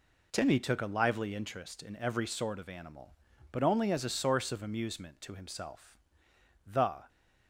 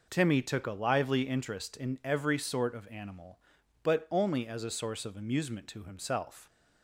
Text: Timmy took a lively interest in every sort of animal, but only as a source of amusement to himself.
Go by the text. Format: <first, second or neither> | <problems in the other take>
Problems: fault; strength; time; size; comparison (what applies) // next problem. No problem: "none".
second | goes on to say "The"; slight; from 6.6 s on; 0.42 s long